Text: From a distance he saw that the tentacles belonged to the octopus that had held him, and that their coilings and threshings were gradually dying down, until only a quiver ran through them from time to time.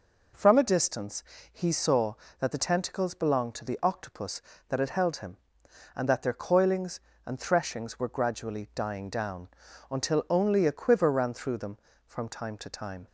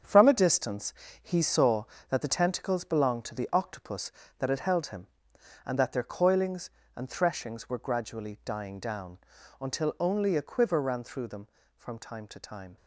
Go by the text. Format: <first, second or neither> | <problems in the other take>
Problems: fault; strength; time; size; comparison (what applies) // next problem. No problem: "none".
first | gets quieter; strong; throughout; 9.5 dB // pauses between "distance" and "he"; slight; at 0.9 s; 0.30 s long; slight in the first